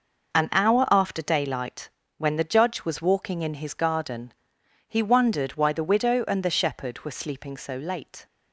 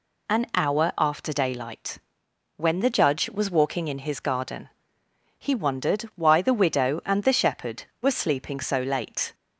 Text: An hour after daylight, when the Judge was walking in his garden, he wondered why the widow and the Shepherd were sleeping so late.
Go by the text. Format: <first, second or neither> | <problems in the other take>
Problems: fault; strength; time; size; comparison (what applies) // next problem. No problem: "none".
second | gets quieter; strong; throughout; 9 dB